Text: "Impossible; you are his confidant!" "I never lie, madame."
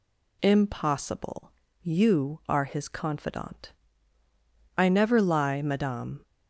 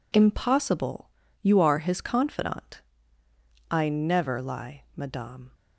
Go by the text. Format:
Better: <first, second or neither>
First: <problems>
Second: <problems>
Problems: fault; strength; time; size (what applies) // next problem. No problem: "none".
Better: neither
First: none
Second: none